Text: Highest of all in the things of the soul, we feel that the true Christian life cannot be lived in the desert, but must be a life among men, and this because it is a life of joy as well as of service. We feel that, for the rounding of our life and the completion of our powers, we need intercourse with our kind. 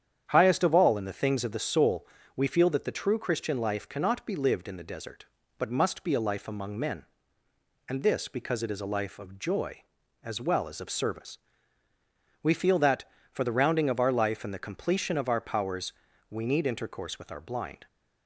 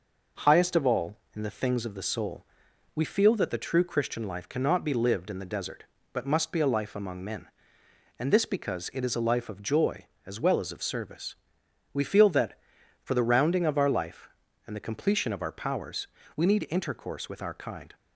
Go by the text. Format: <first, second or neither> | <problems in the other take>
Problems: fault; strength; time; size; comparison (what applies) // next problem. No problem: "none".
second | starts louder than the rest; strong; until 1.3 s; 9 dB // says "blind" for "kind"; at 17.4 s